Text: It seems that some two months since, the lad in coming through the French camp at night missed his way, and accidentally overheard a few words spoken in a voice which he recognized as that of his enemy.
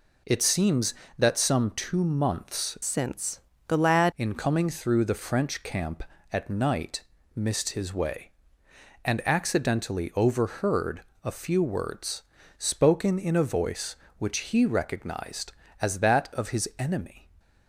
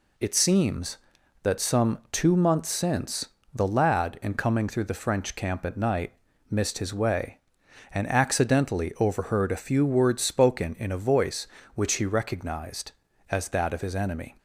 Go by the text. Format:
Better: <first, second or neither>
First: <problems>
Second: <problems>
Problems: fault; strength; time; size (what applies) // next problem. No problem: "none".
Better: second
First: changes voice from "since" to "lad"; from 2.8 to 4.1 s; 1.3 s long // pauses between "night" and "missed"; slight; at 7.0 s; 0.32 s long // pauses between "overheard" and "a"; slight; at 11.0 s; 0.22 s long // pauses between "words" and "spoken"; slight; at 12.2 s; 0.36 s long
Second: pauses between "night" and "missed"; slight; at 6.1 s; 0.36 s long